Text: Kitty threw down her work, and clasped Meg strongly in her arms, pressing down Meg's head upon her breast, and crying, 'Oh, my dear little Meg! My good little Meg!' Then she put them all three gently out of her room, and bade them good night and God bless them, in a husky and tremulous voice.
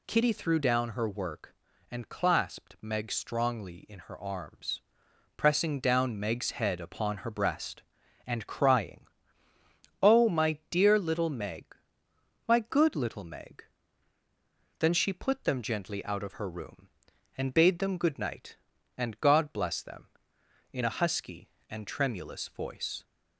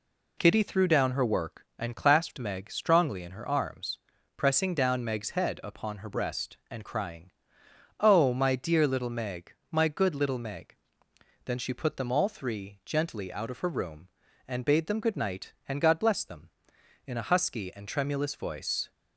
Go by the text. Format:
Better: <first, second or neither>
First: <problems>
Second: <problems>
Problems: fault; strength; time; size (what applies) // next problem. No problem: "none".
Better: second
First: skips "all three"; at 15.6 s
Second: none